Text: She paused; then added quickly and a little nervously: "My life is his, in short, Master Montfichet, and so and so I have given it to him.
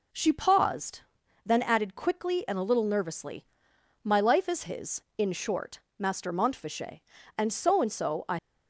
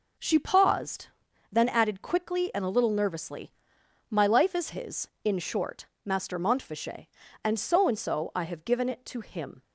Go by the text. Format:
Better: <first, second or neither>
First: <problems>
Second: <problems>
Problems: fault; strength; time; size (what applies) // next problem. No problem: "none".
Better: second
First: stops before "have given it to him"; at 8.3 s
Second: none